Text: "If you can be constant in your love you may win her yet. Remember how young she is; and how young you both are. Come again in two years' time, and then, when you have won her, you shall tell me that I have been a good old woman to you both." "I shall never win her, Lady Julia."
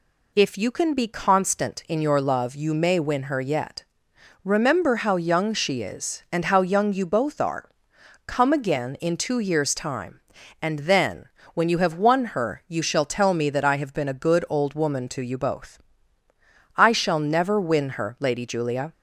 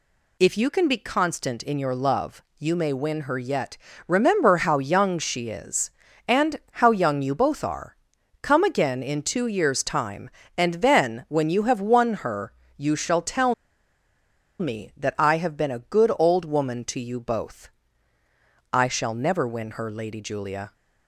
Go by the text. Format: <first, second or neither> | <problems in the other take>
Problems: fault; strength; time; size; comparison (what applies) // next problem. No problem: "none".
first | pauses between "love" and "you"; slight; at 2.4 s; 0.16 s long // pauses between "tell" and "me"; at 13.5 s; 1.0 s long